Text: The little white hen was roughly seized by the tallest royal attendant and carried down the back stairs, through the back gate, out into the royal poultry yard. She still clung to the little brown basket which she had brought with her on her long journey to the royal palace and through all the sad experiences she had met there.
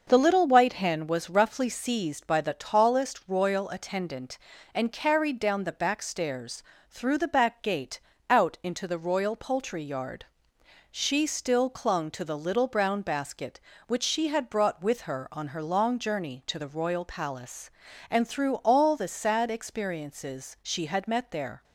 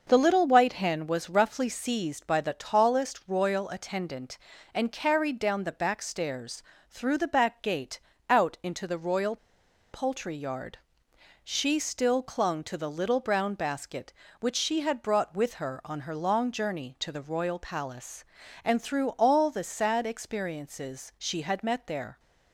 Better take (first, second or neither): first